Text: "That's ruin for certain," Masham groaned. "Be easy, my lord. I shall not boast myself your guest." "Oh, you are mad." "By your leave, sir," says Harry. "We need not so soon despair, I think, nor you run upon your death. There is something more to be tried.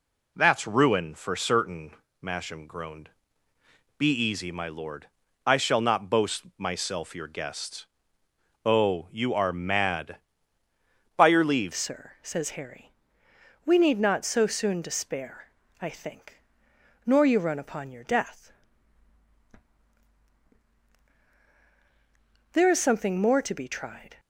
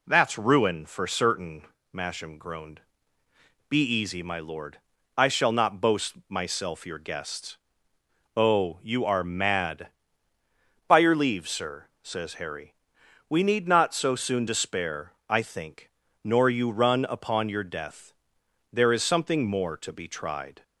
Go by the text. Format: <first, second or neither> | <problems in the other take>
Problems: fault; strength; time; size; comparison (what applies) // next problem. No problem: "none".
second | changes voice at "sir"; from 11.7 s on; 12.4 s long